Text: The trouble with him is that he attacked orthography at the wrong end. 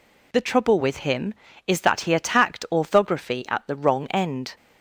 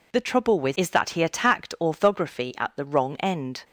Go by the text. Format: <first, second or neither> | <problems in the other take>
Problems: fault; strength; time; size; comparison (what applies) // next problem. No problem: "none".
first | skips "him"; at 0.7 s